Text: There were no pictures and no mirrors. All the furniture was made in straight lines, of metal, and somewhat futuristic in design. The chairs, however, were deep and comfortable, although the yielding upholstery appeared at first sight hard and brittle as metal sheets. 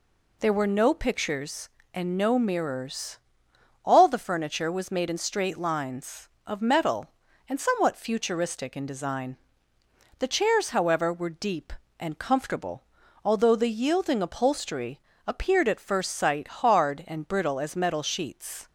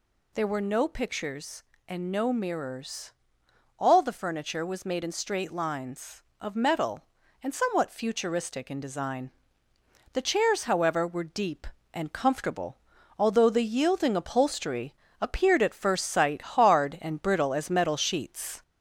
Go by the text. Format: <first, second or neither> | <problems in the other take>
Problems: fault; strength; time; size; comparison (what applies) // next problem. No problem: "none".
first | gets louder; slight; throughout; 2 dB // pauses between "upholstery" and "appeared"; slight; at 14.9 s; 0.26 s long; slight in the first